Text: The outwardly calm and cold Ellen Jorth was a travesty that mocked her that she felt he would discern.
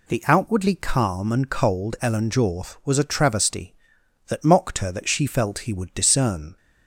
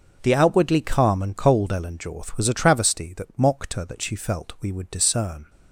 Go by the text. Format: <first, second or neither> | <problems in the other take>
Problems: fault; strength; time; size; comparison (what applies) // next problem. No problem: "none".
first | starts louder than the rest; until 1.2 s; 6.5 dB // says "we" for "he"; at 4.5 s